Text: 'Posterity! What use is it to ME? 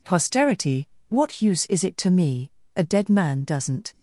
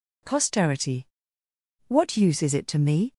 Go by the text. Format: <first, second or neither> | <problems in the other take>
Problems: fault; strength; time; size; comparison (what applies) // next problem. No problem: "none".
second | goes on to say "A dead man doesn't"; noticeable; from 2.7 s on; 1.1 s long